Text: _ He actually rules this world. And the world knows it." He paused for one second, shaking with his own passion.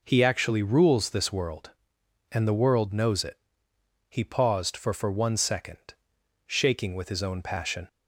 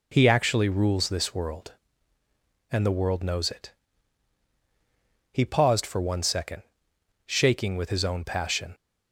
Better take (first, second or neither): second